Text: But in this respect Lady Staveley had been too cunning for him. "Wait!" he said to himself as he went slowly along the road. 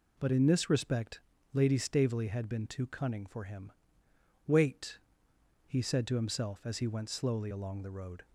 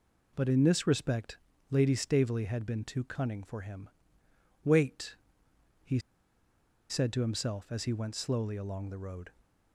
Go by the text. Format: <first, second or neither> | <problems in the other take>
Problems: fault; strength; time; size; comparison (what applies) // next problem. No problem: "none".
first | pauses between "respect" and "Lady"; slight; at 1.3 s; 0.32 s long; slight in the first // pauses between "he" and "said"; noticeable; at 5.9 s; 0.90 s long